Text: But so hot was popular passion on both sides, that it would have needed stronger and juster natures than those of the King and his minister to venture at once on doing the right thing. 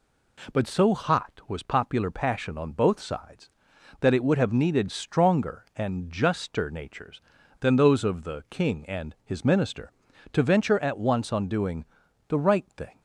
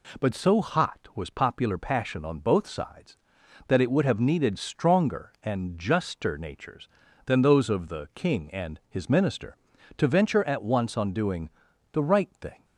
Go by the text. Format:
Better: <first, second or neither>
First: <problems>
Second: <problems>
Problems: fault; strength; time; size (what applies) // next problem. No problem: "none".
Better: neither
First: pauses between "doing" and "the"; at 11.8 s; 0.44 s long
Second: pauses between "doing" and "the"; at 11.4 s; 0.43 s long